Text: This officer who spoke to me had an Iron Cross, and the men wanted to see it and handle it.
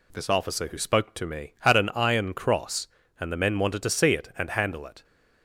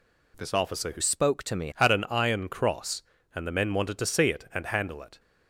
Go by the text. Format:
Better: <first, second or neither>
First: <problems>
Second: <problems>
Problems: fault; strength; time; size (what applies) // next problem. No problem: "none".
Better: first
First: none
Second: changes voice from "spoke" to "me"; from 1.0 to 1.7 s; 0.7 s long